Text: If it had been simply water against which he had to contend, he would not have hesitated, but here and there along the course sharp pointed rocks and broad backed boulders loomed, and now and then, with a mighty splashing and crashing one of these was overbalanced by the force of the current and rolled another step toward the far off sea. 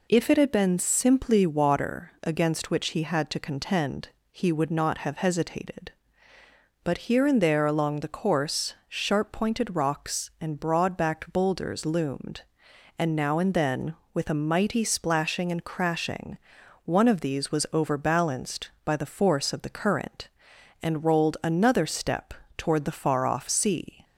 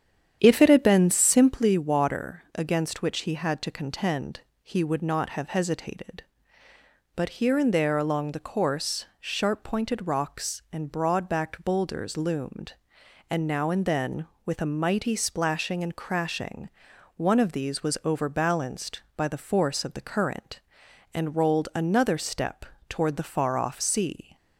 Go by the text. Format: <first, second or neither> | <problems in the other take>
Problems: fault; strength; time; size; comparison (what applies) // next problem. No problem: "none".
first | starts louder than the rest; strong; until 1.6 s; 9 dB // pauses between "course" and "sharp"; slight; at 9.0 s; 0.16 s long; slight in the first // pauses between "crashing" and "one"; noticeable; at 16.6 s; 0.46 s long; noticeable in the first // pauses between "step" and "toward"; slight; at 22.6 s; 0.24 s long; slight in the first